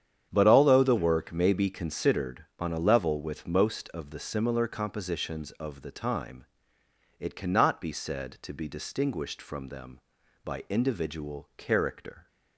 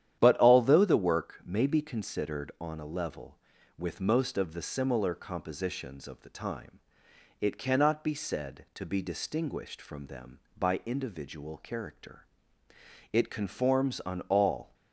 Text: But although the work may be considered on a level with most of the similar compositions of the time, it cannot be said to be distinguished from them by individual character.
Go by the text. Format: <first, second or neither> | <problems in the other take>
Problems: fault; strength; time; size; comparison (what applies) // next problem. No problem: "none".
first | starts louder than the rest; strong; until 1.2 s; 10.5 dB; strong in the first // goes on to say "It conforms on all"; from 13.1 s on; 1.6 s long